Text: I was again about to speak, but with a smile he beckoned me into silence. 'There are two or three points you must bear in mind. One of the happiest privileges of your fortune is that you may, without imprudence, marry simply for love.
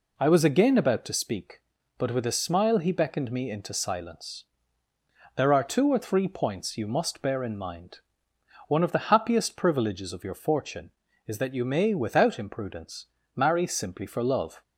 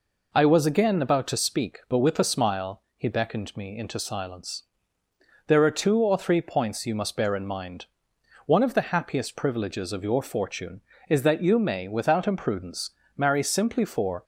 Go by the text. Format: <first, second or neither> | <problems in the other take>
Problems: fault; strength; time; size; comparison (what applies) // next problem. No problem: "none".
first | stops before "love"; at 14.2 s